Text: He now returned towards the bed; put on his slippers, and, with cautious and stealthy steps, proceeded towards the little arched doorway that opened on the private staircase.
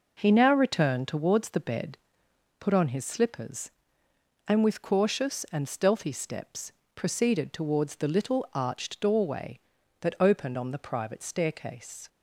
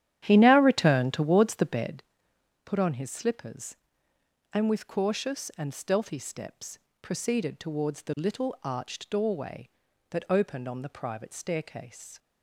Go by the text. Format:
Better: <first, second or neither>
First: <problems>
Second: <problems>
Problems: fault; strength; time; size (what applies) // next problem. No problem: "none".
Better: first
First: none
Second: starts louder than the rest; strong; until 2.0 s; 11 dB